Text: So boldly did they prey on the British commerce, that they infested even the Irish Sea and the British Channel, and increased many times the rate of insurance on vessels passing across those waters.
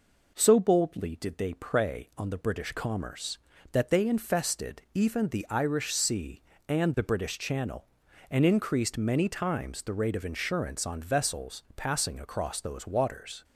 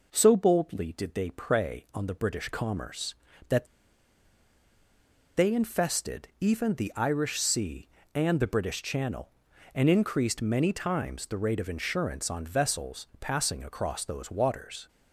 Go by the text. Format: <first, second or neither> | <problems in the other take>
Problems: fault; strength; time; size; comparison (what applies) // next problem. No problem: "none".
first | pauses between "that" and "they"; strong; at 3.6 s; 1.7 s long